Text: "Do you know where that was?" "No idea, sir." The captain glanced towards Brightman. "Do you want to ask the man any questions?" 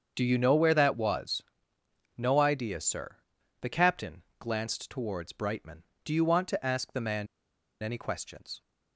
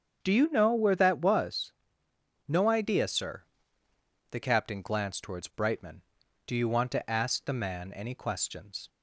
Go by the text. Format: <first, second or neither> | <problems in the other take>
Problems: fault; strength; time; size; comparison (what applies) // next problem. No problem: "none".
second | starts louder than the rest; until 1.1 s; 7 dB; strong in the second // pauses between "captain" and "glanced"; slight; at 4.2 s; 0.18 s long // pauses between "man" and "any"; noticeable; at 7.2 s; 0.56 s long